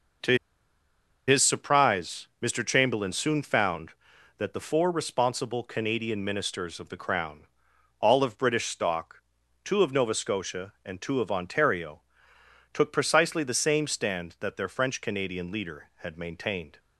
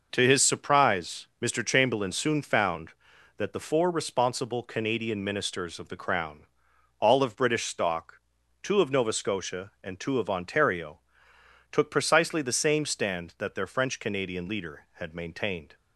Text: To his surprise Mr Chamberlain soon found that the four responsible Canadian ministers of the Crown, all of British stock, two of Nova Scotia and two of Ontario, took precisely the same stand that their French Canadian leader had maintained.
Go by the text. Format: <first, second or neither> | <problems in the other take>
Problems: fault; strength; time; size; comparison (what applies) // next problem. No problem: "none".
second | pauses between "To" and "his"; noticeable; at 0.3 s; 0.91 s long